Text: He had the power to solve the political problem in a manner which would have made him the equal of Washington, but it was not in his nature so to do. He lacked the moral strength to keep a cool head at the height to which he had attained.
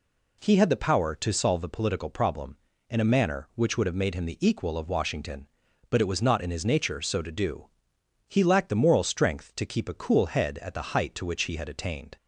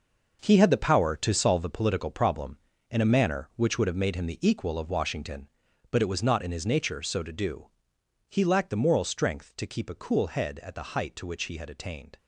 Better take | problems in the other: first | gets quieter; strong; throughout; 10.5 dB

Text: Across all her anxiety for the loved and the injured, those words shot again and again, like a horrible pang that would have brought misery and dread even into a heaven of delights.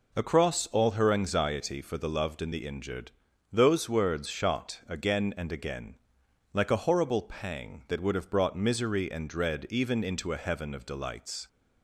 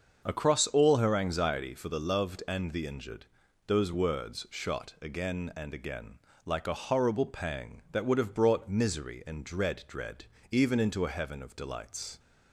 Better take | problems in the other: first | starts louder than the rest; until 1.2 s; 6.5 dB // says "dread" twice; at 9.8 s

